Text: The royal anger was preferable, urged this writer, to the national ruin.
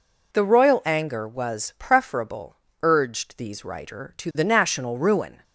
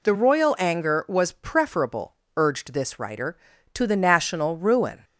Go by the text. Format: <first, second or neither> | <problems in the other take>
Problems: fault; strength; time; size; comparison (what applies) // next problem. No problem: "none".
second | says "these" for "this"; at 3.3 s